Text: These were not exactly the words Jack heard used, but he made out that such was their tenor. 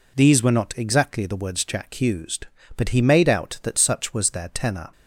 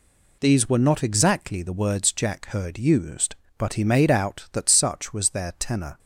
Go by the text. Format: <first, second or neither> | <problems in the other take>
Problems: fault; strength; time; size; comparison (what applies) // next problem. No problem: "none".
second | skips "heard"; at 1.9 s